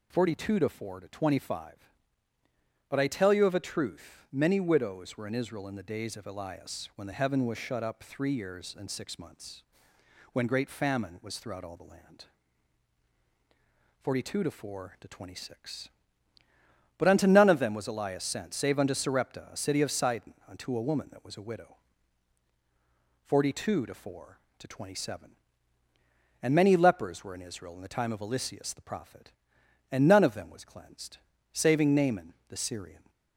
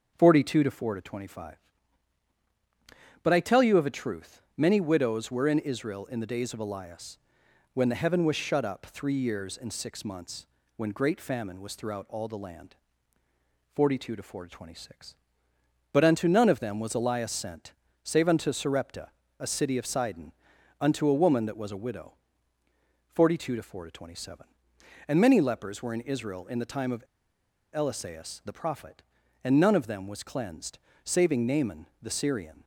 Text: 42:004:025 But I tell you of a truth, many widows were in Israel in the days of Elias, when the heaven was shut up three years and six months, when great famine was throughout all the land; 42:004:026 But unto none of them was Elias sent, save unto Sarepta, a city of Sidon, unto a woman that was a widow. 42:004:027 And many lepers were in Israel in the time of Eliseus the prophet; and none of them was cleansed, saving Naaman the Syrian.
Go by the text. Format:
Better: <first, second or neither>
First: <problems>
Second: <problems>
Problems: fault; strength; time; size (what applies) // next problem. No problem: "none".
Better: first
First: none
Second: starts louder than the rest; until 1.1 s; 7 dB // pauses between "of" and "Eliseus"; noticeable; at 27.0 s; 0.70 s long // pauses between "Naaman" and "the"; slight; at 31.8 s; 0.16 s long